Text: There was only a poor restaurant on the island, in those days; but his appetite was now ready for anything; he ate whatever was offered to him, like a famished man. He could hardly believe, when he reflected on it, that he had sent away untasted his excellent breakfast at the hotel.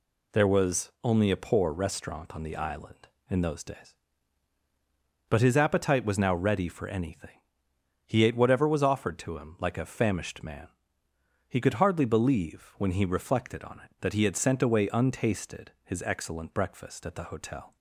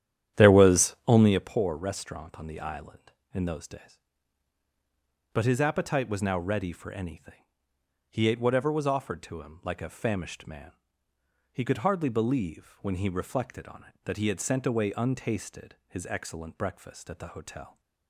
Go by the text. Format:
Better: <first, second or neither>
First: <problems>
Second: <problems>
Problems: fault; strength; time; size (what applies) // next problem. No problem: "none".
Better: first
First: none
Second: starts louder than the rest; strong; until 1.5 s; 10.5 dB